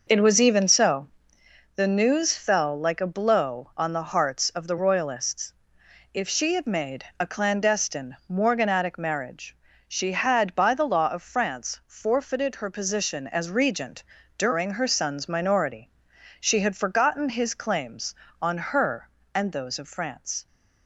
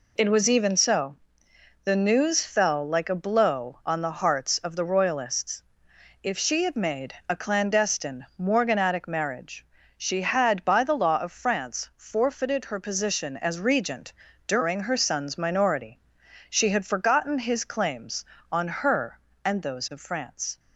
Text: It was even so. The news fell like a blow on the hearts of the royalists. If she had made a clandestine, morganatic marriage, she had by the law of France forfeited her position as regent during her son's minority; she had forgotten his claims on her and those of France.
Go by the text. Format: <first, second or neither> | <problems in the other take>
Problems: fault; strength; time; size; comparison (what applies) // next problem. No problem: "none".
second | starts louder than the rest; noticeable; until 1.6 s; 6 dB // pauses between "made" and "a"; slight; at 7.0 s; 0.16 s long; slight in the second // pauses between "regent" and "during"; slight; at 14.0 s; 0.32 s long; slight in the second